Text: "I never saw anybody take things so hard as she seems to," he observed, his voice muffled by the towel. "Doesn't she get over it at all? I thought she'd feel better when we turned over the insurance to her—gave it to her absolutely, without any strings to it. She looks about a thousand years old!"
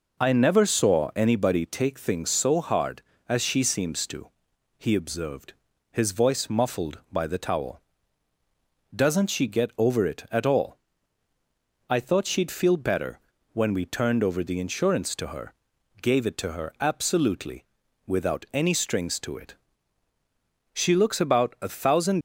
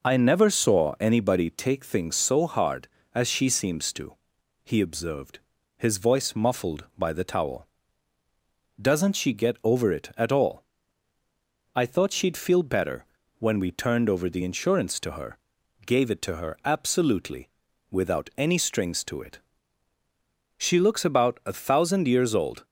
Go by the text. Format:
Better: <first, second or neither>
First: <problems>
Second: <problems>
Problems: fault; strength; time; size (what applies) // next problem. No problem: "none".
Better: second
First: pauses between "better" and "when"; slight; at 13.1 s; 0.32 s long // stops before "years old"; at 22.1 s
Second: pauses between "better" and "when"; slight; at 13.0 s; 0.32 s long